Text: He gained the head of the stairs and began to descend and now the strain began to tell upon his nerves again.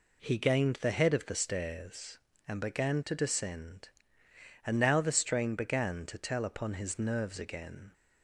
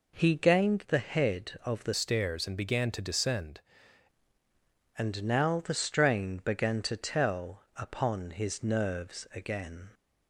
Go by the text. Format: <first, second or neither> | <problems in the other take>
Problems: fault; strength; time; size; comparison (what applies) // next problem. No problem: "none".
first | changes voice from "stairs" to "descend"; from 1.9 to 3.6 s; 1.7 s long